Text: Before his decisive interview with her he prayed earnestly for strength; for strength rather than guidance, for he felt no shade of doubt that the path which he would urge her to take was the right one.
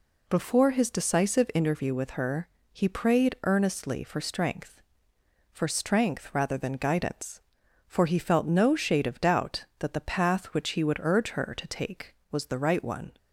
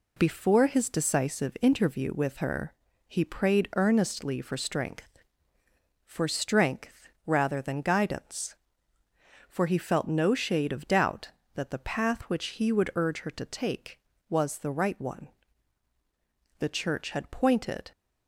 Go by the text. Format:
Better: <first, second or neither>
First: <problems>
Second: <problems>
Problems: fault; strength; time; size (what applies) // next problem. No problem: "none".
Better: first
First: pauses between "her" and "he"; slight; at 2.4 s; 0.26 s long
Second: pauses between "her" and "he"; slight; at 2.7 s; 0.34 s long // pauses between "strength" and "rather"; slight; at 7.0 s; 0.20 s long // goes on to say "The Church had pointed"; from 16.5 s on; 1.3 s long